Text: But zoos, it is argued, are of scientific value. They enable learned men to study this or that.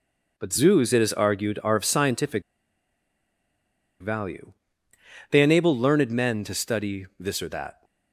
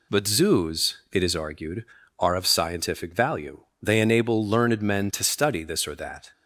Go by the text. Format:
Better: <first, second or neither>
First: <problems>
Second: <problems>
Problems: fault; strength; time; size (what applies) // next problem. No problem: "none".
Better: second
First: pauses between "scientific" and "value"; strong; at 2.4 s; 1.5 s long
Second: none